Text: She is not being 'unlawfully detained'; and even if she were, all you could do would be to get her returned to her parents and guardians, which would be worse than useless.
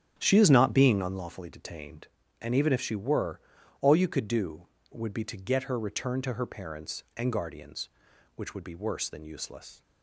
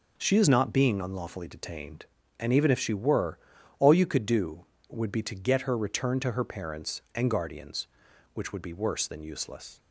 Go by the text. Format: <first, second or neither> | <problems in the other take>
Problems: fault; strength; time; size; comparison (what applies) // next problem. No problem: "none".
second | starts louder than the rest; strong; until 1.3 s; 10 dB